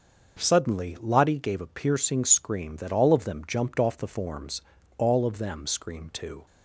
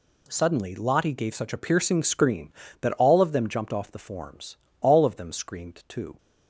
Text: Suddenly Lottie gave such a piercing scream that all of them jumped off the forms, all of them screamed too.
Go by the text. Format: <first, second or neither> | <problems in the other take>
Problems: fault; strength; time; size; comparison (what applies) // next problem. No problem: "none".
second | starts louder than the rest; until 1.4 s; 6 dB // skips "such"; at 1.6 s